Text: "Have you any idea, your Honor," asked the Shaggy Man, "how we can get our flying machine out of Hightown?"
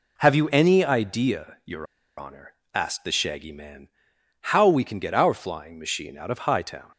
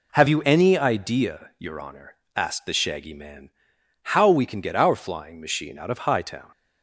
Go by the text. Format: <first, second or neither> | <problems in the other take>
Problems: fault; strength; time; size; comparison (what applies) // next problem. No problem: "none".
second | pauses between "your" and "Honor"; slight; at 1.8 s; 0.33 s long